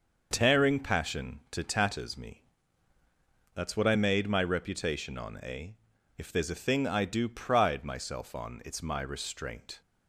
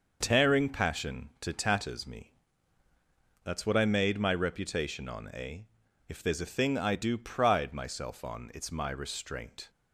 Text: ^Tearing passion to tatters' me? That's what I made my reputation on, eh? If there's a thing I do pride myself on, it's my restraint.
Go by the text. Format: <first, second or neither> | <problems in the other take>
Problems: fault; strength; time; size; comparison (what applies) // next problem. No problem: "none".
neither | starts louder than the rest; the same in both